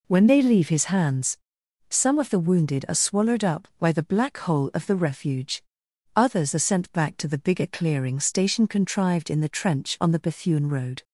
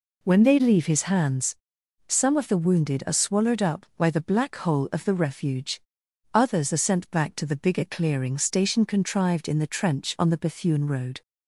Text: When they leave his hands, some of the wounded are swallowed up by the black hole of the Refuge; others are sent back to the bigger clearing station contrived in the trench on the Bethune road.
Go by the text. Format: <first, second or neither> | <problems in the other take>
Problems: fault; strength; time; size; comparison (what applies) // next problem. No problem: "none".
neither | none